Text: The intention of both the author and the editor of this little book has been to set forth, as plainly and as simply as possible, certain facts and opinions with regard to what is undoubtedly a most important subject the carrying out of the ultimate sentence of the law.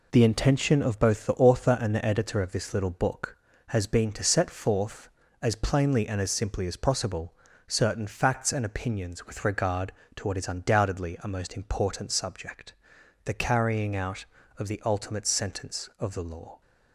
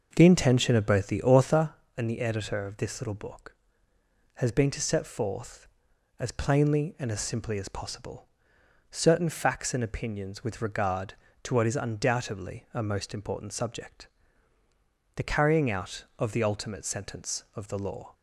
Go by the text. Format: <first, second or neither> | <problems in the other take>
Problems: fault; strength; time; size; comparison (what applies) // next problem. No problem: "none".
first | starts louder than the rest; noticeable; until 1.8 s; 6 dB // pauses between "subject" and "the"; at 14.0 s; 1.0 s long; noticeable in the first